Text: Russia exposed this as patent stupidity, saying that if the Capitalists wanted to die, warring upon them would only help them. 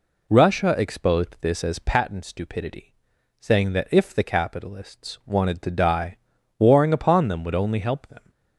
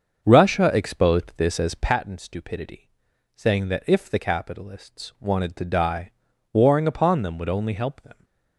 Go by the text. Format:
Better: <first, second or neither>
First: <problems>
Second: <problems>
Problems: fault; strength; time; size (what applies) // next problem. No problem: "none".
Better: first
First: none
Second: starts louder than the rest; until 2.0 s; 6.5 dB